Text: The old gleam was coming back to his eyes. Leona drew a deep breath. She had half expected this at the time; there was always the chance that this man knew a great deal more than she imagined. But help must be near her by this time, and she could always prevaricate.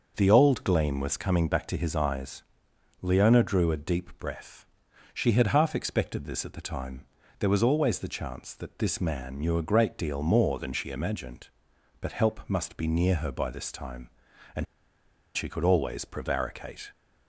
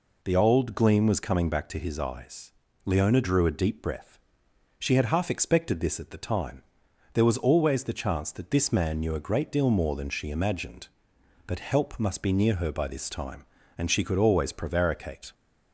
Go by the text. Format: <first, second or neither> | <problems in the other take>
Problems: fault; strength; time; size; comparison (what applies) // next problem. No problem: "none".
second | starts louder than the rest; noticeable; until 1.1 s; 6 dB // pauses between "and" and "she"; noticeable; at 14.6 s; 0.69 s long